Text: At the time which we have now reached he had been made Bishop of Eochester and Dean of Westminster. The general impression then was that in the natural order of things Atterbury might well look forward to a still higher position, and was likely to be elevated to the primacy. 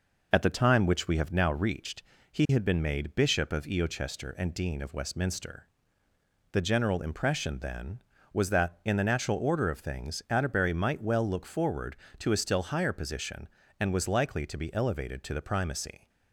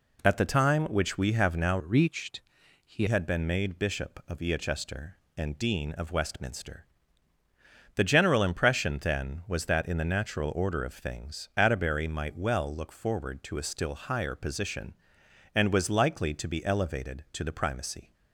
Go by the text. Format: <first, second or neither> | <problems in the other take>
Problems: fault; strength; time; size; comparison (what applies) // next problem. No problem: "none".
first | changes voice from "reached" to "he"; from 1.7 to 3.0 s; 1.3 s long // pauses between "reached" and "he"; at 2.4 s; 0.44 s long; slight in the first